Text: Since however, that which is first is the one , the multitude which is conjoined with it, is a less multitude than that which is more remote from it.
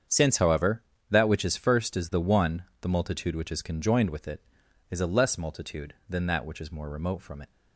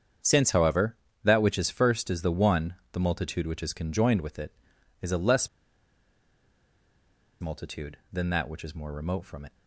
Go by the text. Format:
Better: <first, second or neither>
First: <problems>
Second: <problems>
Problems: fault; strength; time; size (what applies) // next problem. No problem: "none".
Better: first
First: starts louder than the rest; strong; until 1.3 s; 8 dB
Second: starts louder than the rest; strong; until 1.5 s; 8 dB // pauses between "less" and "multitude"; strong; at 5.4 s; 1.9 s long